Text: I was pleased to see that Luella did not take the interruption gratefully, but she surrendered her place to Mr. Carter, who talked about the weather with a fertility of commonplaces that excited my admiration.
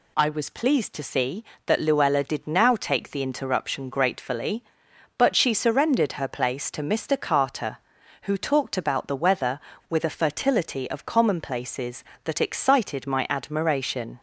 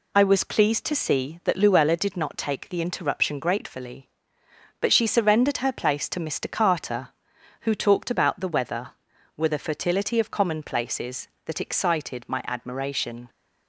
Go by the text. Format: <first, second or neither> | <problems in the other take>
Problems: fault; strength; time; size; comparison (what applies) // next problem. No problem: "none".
second | says "now" for "not"; at 2.4 s